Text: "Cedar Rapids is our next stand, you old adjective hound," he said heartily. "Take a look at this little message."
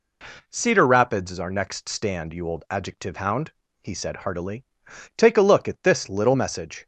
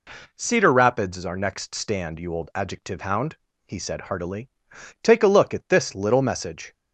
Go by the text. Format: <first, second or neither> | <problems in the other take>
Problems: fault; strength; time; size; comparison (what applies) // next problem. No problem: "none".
neither | none